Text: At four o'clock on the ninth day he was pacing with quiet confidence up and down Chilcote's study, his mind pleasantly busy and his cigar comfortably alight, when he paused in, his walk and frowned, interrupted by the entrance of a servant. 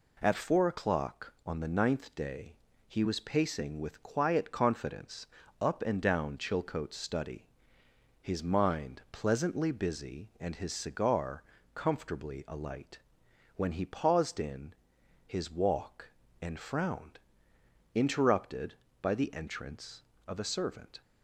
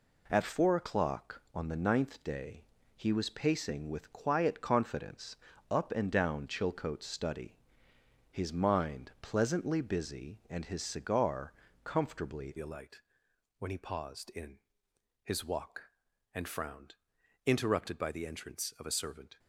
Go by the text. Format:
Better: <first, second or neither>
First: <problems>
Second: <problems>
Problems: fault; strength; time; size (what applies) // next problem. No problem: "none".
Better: first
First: pauses between "day" and "he"; slight; at 2.5 s; 0.32 s long // pauses between "confidence" and "up"; slight; at 5.2 s; 0.34 s long // pauses between "cigar" and "comfortably"; slight; at 11.4 s; 0.32 s long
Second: pauses between "day" and "he"; slight; at 2.6 s; 0.32 s long // pauses between "confidence" and "up"; slight; at 5.3 s; 0.34 s long // pauses between "cigar" and "comfortably"; slight; at 11.5 s; 0.32 s long // changes voice at "alight"; from 12.5 s on; 6.8 s long